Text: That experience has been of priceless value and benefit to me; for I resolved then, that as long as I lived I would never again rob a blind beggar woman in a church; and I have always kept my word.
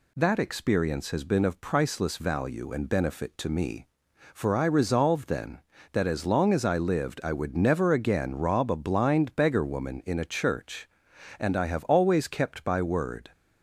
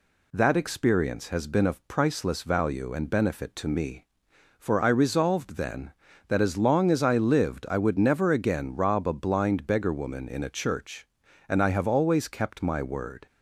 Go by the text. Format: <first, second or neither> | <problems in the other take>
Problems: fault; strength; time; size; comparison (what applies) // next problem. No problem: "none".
second | says "by" for "my"; at 12.6 s